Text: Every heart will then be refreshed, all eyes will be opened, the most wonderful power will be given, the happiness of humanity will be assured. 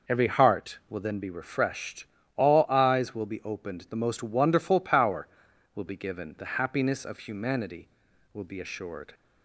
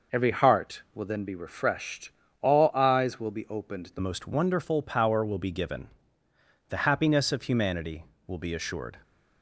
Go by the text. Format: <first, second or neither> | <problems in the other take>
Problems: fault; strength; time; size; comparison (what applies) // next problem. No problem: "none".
first | changes voice at "most"; from 3.9 s on; 5.0 s long